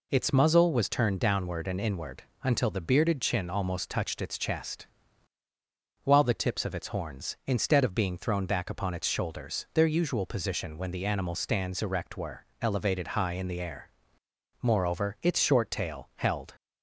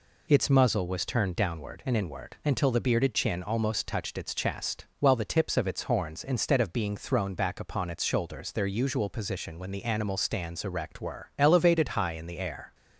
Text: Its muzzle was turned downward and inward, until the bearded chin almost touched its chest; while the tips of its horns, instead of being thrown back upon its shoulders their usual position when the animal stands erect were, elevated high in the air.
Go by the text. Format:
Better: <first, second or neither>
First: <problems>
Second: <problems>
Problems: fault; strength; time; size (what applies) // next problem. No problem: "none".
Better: second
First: goes on to say "Moreover its short tail held"; strong; from 14.6 s on; 1.9 s long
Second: none